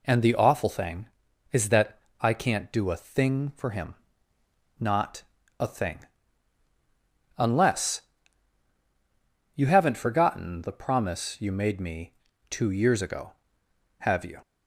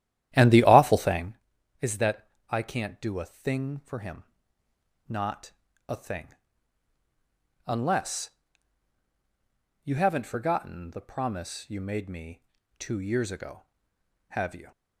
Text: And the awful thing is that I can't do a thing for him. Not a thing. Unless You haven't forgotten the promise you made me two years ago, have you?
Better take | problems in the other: first | starts louder than the rest; strong; until 1.4 s; 12 dB // pauses between "that" and "I"; slight; at 2.2 s; 0.22 s long; slight in the first // pauses between "Not" and "a"; slight; at 5.5 s; 0.36 s long; slight in the first // pauses between "Unless" and "You"; strong; at 8.3 s; 1.5 s long; strong in the first // pauses between "me" and "two"; slight; at 12.4 s; 0.34 s long; slight in the first

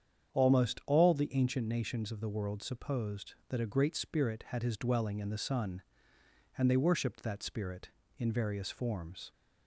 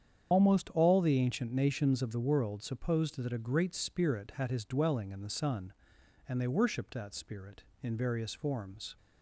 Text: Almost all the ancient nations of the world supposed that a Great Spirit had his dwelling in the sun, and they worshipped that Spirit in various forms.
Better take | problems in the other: first | loses the start of "Almost"; at 0.3 s; 45 ms // starts louder than the rest; strong; until 1.3 s; 8.5 dB; strong in the first

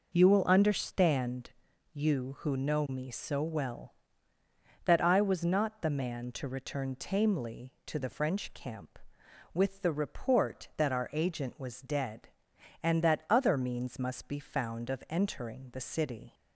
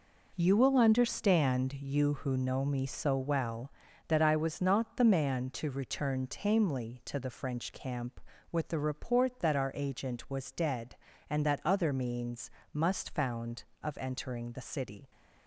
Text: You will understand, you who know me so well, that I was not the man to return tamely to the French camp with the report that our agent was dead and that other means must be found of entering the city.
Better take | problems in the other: first | pauses between "means" and "must"; slight; at 12.4 s; 0.24 s long // skips "be"; at 13.1 s

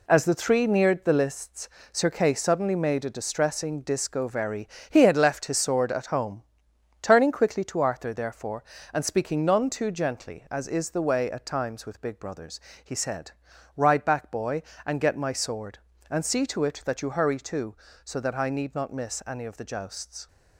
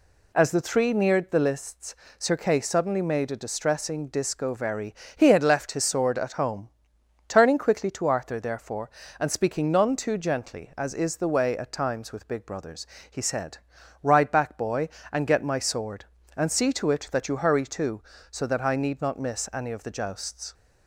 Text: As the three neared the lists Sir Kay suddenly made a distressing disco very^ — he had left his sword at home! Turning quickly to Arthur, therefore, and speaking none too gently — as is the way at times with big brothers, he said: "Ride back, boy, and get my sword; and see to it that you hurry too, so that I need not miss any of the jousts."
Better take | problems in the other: second | gets quieter; throughout; 7 dB // pauses between "lists" and "Sir"; slight; at 1.6 s; 0.24 s long; slight in the second

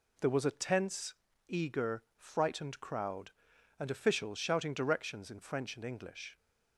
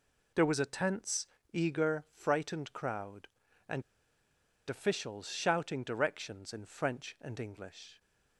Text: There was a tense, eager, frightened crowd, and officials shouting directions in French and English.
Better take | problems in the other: first | pauses between "and" and "officials"; noticeable; at 3.8 s; 0.87 s long

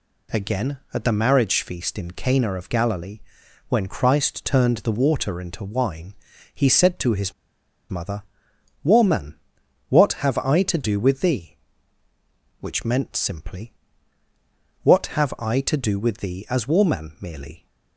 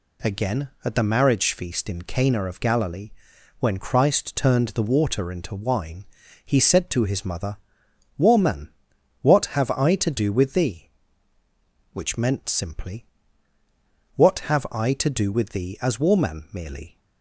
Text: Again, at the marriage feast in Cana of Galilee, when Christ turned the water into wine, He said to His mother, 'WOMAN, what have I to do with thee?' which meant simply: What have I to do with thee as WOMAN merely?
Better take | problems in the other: second | pauses between "His" and "mother"; noticeable; at 7.3 s; 0.57 s long

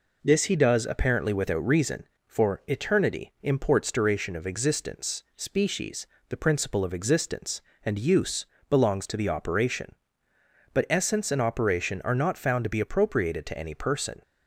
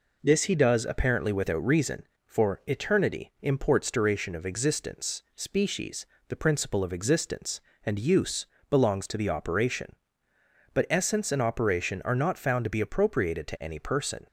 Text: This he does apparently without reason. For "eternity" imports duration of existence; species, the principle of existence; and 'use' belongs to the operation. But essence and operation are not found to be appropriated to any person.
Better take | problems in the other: neither | pauses between "use" and "belongs"; slight; the same in both

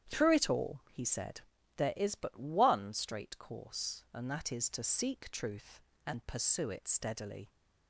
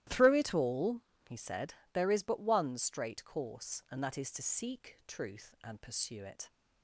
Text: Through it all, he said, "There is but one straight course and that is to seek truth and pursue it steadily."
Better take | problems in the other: first | starts louder than the rest; strong; until 1.3 s; 14 dB; strong in the first // stops before "steadily"; at 6.4 s

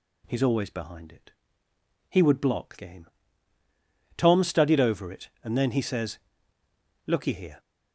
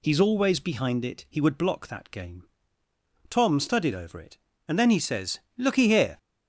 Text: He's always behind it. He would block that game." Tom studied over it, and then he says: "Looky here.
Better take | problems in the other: second | skips "that"; at 2.7 s

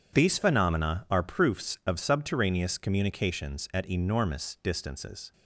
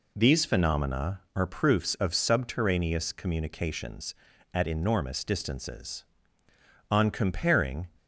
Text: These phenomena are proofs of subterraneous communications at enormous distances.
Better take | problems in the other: first | goes on to say "On comparing"; noticeable; from 6.8 s on; 1.0 s long

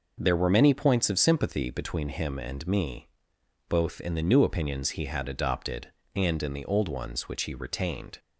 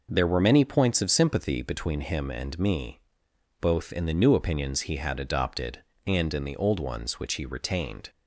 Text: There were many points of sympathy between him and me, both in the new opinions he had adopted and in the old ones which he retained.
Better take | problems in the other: neither | none

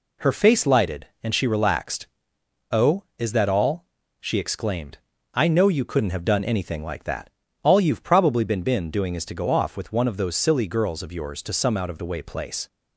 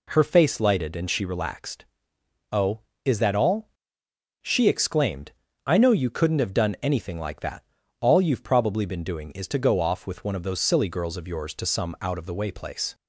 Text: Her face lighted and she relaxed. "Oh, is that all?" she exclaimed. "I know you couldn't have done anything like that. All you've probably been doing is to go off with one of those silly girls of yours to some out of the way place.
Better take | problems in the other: second | says "been" twice; at 8.6 s

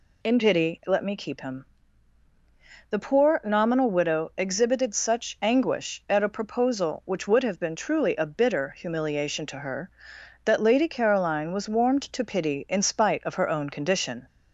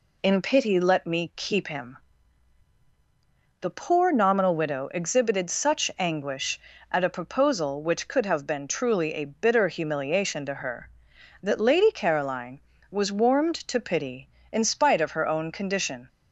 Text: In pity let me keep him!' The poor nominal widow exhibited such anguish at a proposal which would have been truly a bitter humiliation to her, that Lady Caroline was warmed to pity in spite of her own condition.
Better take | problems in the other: first | says "could" for "would"; at 8.0 s

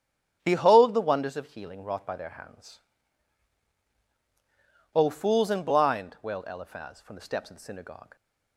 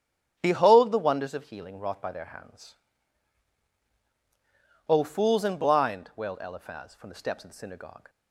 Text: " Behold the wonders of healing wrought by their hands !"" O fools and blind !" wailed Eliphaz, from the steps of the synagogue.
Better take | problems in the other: neither | starts louder than the rest; strong; the same in both

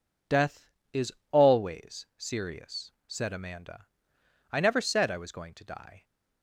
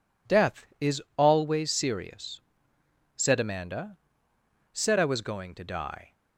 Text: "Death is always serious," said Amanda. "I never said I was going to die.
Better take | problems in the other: first | pauses between "is" and "always"; slight; at 1.0 s; 0.16 s long; slight in the first // skips "I never"; at 4.3 s

